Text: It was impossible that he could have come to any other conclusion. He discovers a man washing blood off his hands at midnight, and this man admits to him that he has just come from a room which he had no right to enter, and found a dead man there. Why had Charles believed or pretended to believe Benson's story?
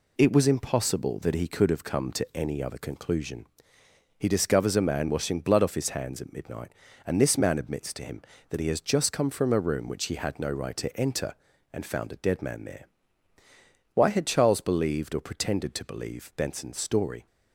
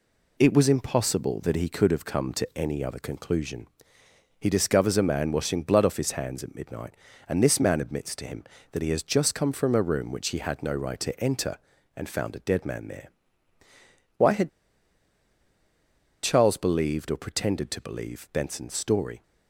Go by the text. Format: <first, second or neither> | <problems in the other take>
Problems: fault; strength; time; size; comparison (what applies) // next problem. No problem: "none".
first | pauses between "had" and "Charles"; strong; at 14.4 s; 1.7 s long